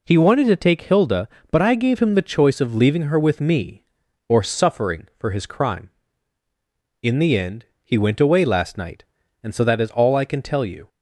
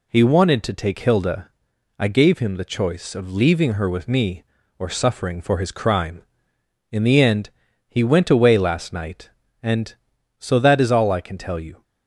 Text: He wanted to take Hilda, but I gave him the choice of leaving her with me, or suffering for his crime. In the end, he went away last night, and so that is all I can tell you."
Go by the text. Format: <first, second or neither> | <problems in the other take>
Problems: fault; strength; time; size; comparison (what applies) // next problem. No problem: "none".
first | skips "but"; at 1.7 s